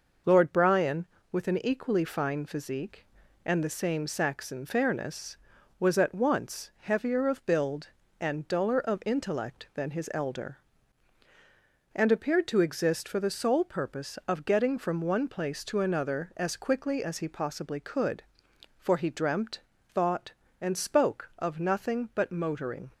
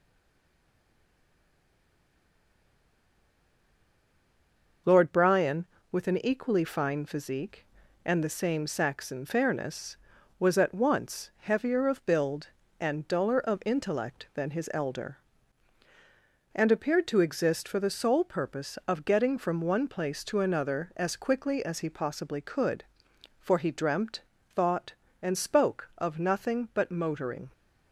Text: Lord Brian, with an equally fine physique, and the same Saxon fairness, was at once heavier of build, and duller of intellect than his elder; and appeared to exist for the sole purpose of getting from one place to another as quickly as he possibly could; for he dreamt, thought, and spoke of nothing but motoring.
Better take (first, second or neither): first